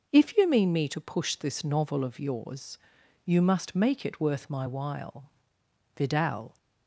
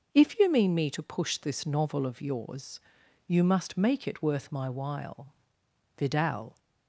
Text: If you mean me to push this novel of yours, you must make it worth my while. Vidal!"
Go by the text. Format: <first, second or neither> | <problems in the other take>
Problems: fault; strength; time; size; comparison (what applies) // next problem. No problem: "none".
neither | starts louder than the rest; noticeable; the same in both